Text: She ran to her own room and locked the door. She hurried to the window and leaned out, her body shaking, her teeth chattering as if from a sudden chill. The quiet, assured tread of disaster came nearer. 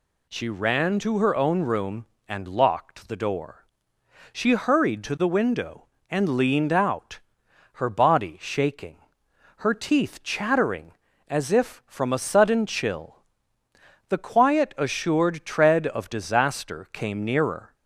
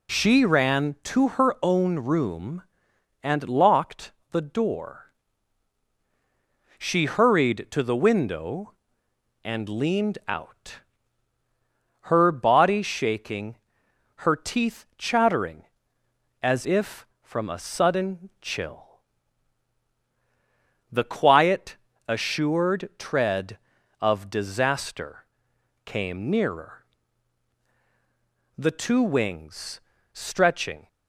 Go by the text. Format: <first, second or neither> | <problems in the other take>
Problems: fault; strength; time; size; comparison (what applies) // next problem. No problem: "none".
first | pauses between "locked" and "the"; slight; at 4.1 s; 0.22 s long // pauses between "disaster" and "came"; noticeable; at 25.2 s; 0.58 s long // goes on to say "The two wings stretching"; strong; from 28.5 s on; 2.3 s long